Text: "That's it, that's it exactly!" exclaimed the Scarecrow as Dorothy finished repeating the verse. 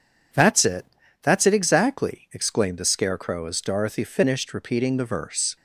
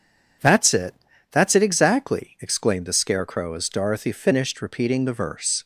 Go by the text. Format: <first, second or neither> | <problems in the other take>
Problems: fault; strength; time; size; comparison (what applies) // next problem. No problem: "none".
neither | none